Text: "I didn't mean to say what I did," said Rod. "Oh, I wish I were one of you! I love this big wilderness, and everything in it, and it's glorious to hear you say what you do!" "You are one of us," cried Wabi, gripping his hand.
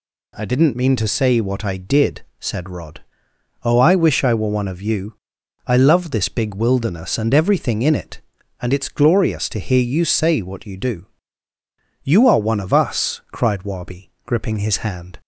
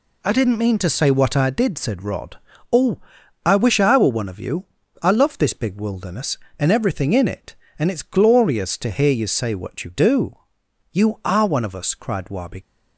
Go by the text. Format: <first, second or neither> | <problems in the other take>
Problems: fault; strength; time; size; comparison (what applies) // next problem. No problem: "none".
first | stops before "gripping his hand"; at 12.6 s